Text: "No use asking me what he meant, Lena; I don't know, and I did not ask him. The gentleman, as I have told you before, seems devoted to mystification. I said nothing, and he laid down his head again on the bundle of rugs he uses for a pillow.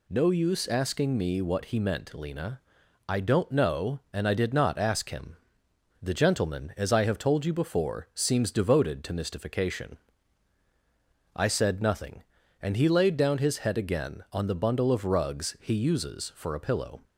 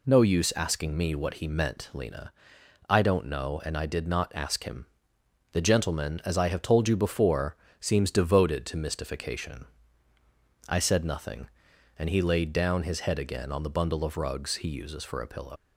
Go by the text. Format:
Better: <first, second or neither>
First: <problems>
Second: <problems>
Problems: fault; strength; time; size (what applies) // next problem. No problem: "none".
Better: first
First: none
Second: leaves "pillow" unfinished; at 15.5 s; 120 ms